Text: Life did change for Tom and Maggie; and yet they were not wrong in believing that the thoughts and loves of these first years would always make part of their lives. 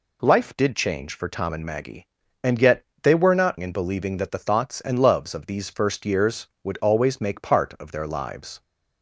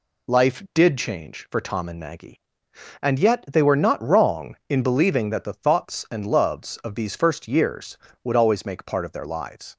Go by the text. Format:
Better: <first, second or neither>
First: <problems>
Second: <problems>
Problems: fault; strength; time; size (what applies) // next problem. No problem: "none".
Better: second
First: pauses between "yet" and "they"; slight; at 2.8 s; 0.16 s long // skips "wrong"; at 3.5 s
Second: none